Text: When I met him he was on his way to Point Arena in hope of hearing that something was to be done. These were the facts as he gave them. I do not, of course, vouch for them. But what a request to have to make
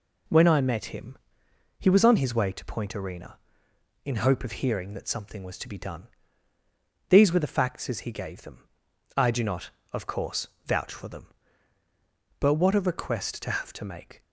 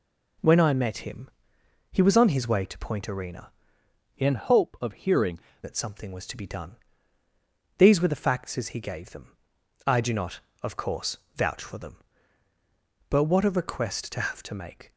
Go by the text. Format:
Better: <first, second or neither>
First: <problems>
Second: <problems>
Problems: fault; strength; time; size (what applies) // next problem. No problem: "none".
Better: first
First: pauses between "him" and "he"; noticeable; at 1.1 s; 0.62 s long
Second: pauses between "him" and "he"; noticeable; at 1.2 s; 0.62 s long // changes voice from "in" to "hearing"; from 4.1 to 5.3 s; 1.2 s long